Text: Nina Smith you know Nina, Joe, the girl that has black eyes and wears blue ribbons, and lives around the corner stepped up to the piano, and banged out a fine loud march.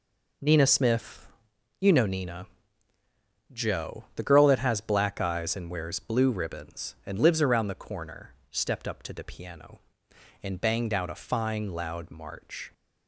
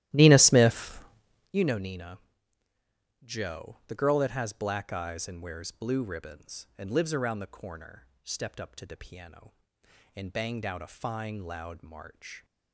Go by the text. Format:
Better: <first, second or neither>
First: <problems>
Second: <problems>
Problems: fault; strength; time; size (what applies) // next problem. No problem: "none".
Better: first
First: pauses between "Smith" and "you"; noticeable; at 1.2 s; 0.54 s long // pauses between "corner" and "stepped"; slight; at 8.3 s; 0.16 s long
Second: starts louder than the rest; strong; until 1.6 s; 14.5 dB // pauses between "Smith" and "you"; noticeable; at 0.9 s; 0.54 s long // pauses between "corner" and "stepped"; slight; at 8.0 s; 0.16 s long